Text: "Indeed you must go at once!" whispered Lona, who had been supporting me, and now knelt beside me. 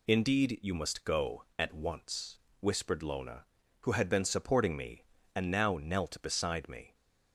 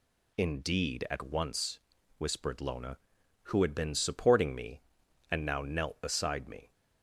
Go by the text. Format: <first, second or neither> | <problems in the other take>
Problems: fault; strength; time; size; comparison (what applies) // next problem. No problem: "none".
first | skips "you must go"; at 1.0 s